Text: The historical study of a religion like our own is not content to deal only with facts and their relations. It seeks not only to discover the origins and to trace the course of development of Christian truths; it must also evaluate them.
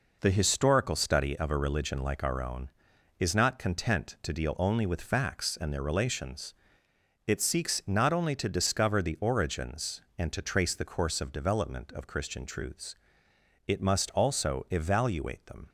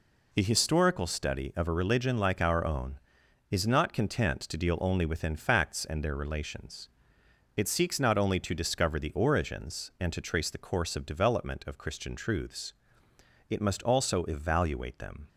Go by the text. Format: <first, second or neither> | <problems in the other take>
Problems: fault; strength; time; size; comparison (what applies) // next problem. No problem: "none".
first | says "within" for "with"; at 5.0 s